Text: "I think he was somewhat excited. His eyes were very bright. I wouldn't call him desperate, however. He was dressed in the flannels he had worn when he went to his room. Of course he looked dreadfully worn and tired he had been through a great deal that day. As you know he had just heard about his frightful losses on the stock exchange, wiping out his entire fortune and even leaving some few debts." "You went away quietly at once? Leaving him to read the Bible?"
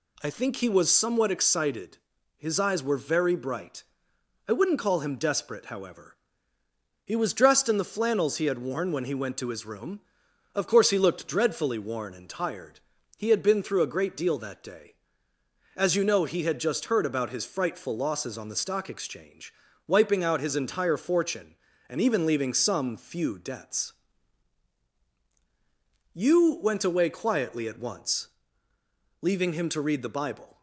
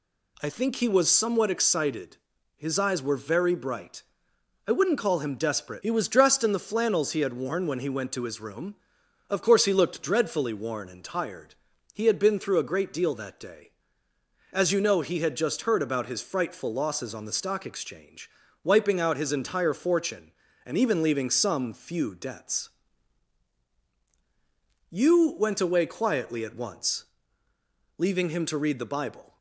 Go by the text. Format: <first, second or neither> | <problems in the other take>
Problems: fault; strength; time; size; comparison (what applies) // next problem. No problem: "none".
first | skips "however"; at 5.8 s // pauses between "tired" and "he"; at 11.5 s; 0.38 s long; also in the first